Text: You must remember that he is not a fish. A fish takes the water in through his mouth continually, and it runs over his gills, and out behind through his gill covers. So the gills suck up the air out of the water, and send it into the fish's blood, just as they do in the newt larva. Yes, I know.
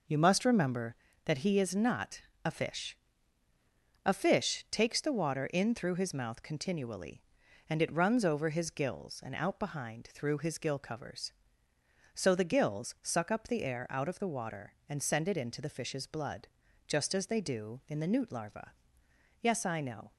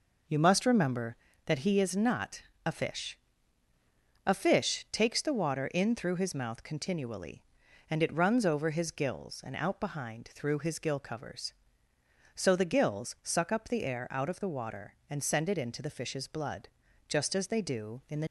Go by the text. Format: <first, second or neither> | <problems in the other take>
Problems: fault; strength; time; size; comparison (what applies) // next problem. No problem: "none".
first | pauses between "not" and "a"; slight; at 2.4 s; 0.24 s long; slight in the first // stops before "newt larva Yes I know"; at 18.2 s